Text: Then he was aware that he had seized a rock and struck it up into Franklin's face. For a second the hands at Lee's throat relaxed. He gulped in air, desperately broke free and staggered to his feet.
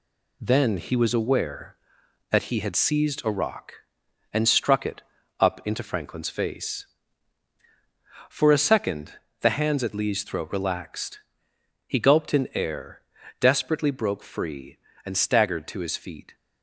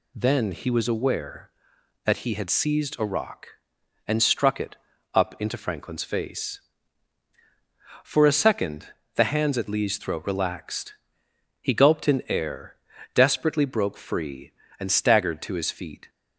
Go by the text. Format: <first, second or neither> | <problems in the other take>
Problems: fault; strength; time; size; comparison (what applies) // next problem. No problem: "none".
second | gets quieter; throughout; 6 dB // pauses between "it" and "up"; at 5.0 s; 0.38 s long; also in the second // pauses between "second" and "the"; slight; at 9.1 s; 0.28 s long; slight in the second